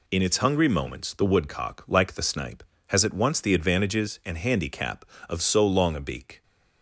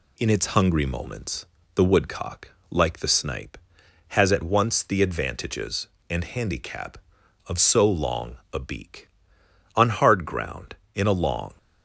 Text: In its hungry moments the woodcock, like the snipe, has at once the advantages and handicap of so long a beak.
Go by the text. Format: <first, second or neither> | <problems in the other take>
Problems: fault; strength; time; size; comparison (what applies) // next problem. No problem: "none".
first | pauses between "moments" and "the"; slight; at 1.4 s; 0.30 s long // pauses between "long" and "a"; slight; at 8.3 s; 0.18 s long // goes on to say "On hard ground in a long"; strong; from 9.7 s on; 1.7 s long